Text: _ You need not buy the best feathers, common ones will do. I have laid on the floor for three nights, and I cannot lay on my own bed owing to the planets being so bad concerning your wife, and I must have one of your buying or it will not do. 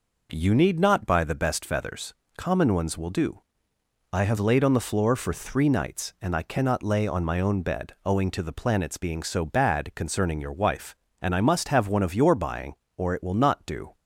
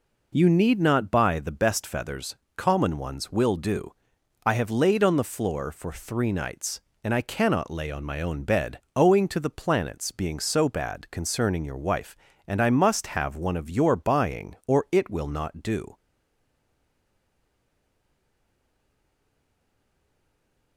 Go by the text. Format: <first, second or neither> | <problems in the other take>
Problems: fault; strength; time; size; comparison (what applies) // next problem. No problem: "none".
first | pauses between "bed" and "owing"; slight; at 8.7 s; 0.16 s long // stays silent after the last word; strong; from 15.9 s on; 4.8 s long